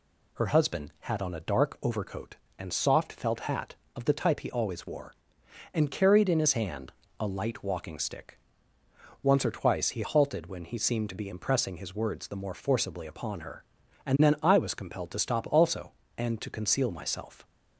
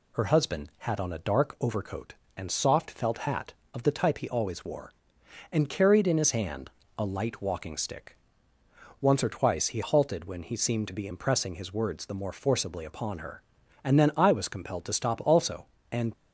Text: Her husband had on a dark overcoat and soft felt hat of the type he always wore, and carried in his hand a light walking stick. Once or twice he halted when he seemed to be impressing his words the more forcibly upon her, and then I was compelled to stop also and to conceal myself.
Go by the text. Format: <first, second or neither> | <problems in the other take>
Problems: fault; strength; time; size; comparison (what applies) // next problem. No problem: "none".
first | pauses between "hand" and "a"; slight; at 6.6 s; 0.26 s long; slight in the first // stops before "to conceal myself"; at 16.1 s